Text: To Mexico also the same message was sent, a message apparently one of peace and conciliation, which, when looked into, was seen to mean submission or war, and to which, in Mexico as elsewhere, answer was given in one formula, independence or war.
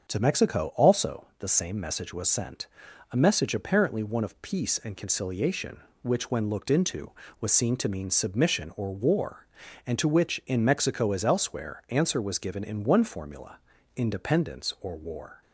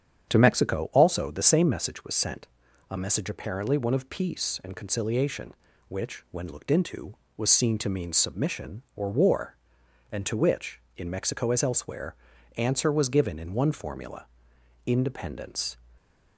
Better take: first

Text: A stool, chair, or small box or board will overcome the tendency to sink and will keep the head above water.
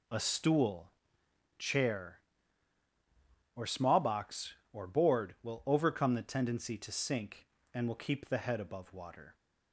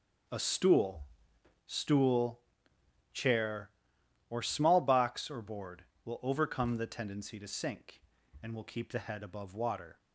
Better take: first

